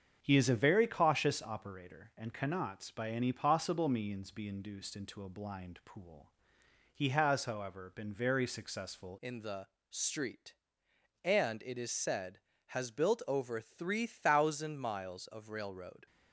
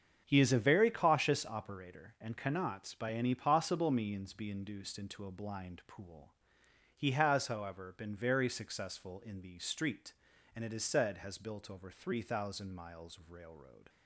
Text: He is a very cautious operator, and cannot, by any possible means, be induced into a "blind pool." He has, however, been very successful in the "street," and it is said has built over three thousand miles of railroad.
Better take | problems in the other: second | starts louder than the rest; strong; until 1.2 s; 7.5 dB; strong in the second // changes voice at "in"; from 9.1 s on; 6.9 s long // pauses between "the" and "street"; slight; at 9.6 s; 0.22 s long

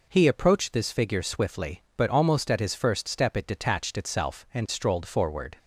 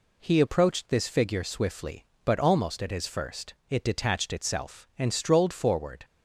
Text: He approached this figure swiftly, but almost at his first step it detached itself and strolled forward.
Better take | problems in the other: first | skips "step"; at 3.6 s

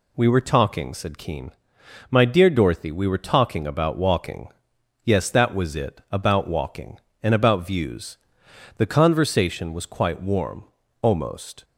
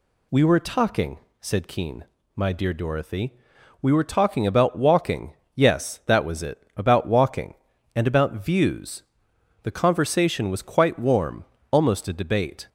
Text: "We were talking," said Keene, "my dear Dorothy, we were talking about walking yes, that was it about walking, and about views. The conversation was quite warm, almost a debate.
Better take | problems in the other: second | pauses between "walking" and "yes"; noticeable; at 4.4 s; 0.54 s long; slight in the second // stops before "a debate"; at 11.6 s

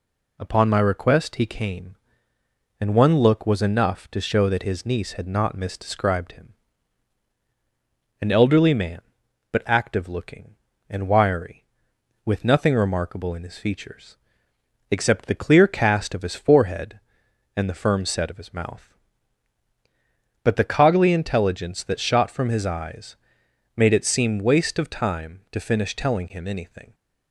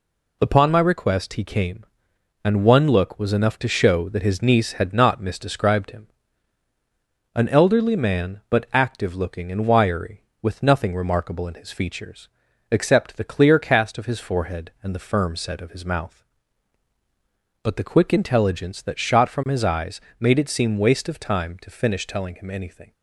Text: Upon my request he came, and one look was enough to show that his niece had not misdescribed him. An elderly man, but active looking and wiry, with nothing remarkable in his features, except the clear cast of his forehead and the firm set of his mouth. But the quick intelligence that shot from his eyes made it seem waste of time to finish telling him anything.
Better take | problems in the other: second | says "coggly" for "quick"; at 20.6 s // pauses between "eyes" and "made"; noticeable; at 23.1 s; 0.60 s long; slight in the second

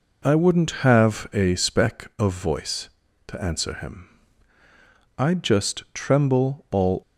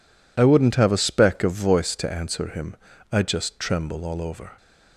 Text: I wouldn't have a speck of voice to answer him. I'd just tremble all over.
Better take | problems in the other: second | stops before "over"; at 7.0 s

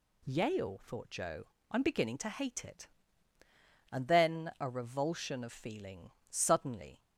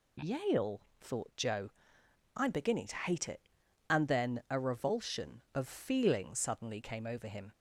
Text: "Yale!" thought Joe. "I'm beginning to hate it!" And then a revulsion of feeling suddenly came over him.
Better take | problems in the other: second | pauses between "feeling" and "suddenly"; slight; at 6.1 s; 0.18 s long // stops before "came over him"; at 7.0 s

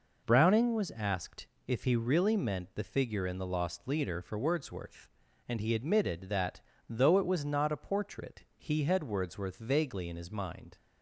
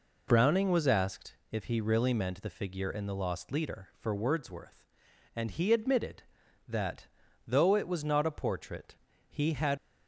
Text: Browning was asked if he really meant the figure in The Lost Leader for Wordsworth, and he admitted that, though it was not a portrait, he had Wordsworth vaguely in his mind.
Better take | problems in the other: first | pauses between "asked" and "if"; slight; at 1.3 s; 0.18 s long; slight in the first // stops before "Wordsworth vaguely in his mind"; at 9.7 s

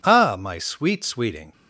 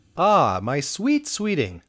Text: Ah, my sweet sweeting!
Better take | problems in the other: neither | none

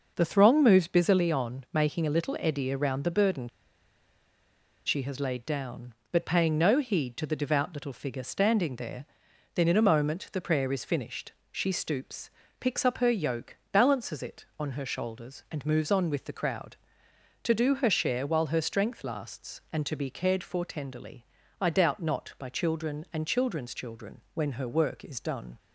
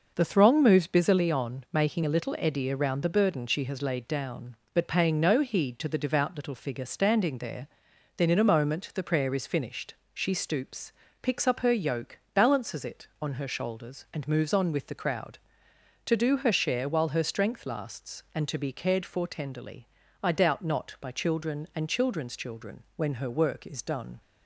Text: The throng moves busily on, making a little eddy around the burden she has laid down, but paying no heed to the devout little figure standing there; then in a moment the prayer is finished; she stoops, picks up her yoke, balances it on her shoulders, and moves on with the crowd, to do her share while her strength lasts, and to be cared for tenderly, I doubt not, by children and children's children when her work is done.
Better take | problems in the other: second | pauses between "burden" and "she"; strong; at 3.4 s; 1.3 s long

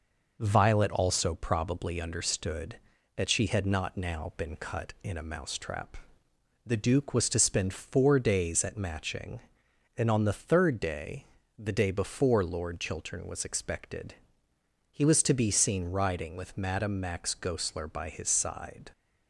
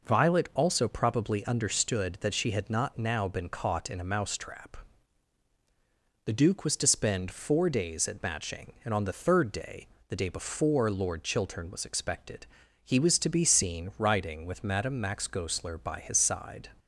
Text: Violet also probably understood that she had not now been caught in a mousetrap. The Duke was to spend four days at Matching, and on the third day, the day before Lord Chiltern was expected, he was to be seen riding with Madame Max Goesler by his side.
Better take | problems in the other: second | says "cut" for "caught"; at 4.5 s

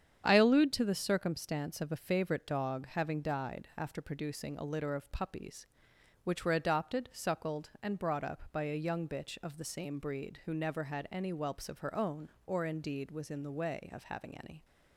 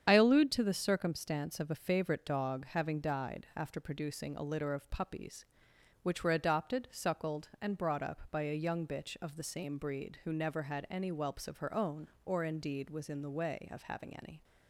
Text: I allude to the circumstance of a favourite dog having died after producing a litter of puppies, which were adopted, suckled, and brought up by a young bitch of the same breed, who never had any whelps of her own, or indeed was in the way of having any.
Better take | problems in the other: first | loses the start of "I"; at 0.0 s; 45 ms // starts louder than the rest; strong; until 1.0 s; 8.5 dB; strong in the first

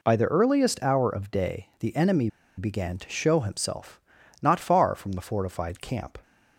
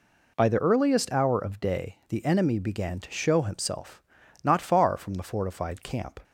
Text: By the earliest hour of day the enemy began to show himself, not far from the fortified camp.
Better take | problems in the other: second | pauses between "enemy" and "began"; slight; at 2.2 s; 0.28 s long

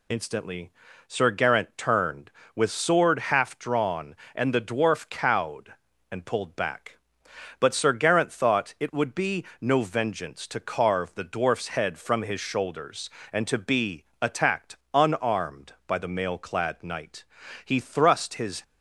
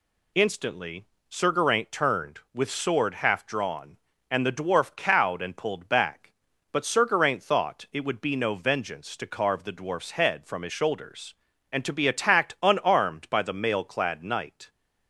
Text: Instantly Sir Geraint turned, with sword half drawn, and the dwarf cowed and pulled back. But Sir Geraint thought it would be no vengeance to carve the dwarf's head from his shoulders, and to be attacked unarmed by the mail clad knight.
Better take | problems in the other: second | pauses between "Instantly" and "Sir"; slight; at 0.7 s; 0.36 s long; slight in the second // pauses between "be" and "no"; slight; at 9.4 s; 0.16 s long // pauses between "be" and "attacked"; slight; at 14.0 s; 0.18 s long // pauses between "attacked" and "unarmed"; slight; at 14.7 s; 0.18 s long // goes on to say "He thrust his"; noticeable; from 17.6 s on; 0.98 s long

